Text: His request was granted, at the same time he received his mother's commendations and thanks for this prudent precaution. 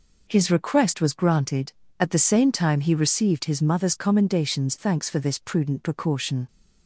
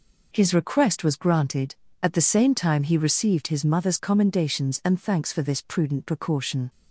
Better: second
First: skips "and"; at 4.7 s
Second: none

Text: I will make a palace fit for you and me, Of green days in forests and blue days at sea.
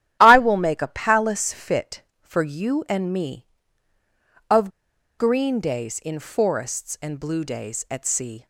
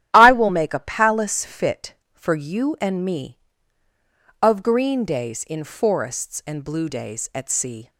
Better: second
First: starts louder than the rest; strong; until 1.2 s; 11.5 dB // pauses between "Of" and "green"; noticeable; at 4.6 s; 0.48 s long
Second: starts louder than the rest; strong; until 1.1 s; 11 dB

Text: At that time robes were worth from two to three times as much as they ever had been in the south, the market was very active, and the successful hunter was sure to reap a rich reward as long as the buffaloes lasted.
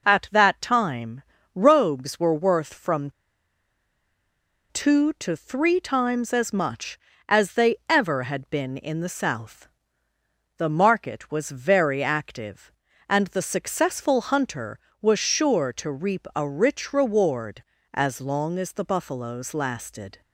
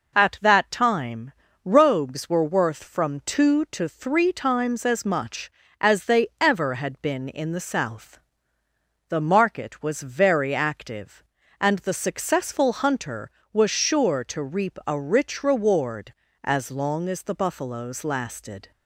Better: second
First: pauses between "time" and "robes"; slight; at 1.2 s; 0.34 s long // pauses between "from" and "two"; strong; at 3.1 s; 1.6 s long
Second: pauses between "time" and "robes"; slight; at 1.3 s; 0.34 s long

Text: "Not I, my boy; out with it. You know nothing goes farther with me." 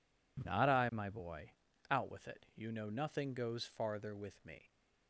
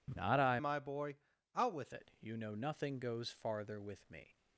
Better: first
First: none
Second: changes voice from "my" to "with"; from 0.5 to 1.9 s; 1.4 s long

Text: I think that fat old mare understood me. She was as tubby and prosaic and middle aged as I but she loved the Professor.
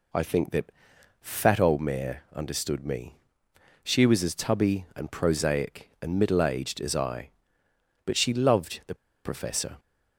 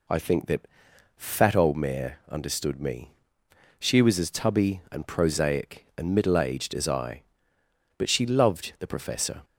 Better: second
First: pauses between "that" and "fat"; noticeable; at 0.7 s; 0.50 s long // pauses between "the" and "Professor"; slight; at 8.9 s; 0.29 s long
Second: pauses between "that" and "fat"; noticeable; at 0.6 s; 0.50 s long

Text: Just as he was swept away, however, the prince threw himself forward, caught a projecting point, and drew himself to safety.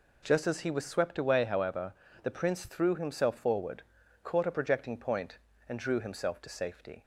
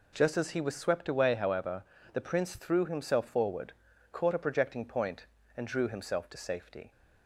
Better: neither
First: none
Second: none

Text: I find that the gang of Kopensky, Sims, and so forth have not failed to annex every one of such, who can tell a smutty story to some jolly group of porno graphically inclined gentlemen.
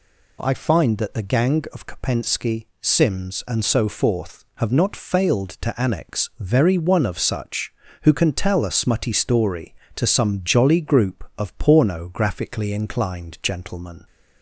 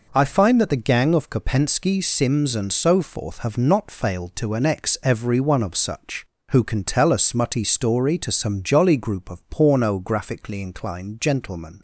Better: second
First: says "very" for "every"; at 6.3 s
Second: none

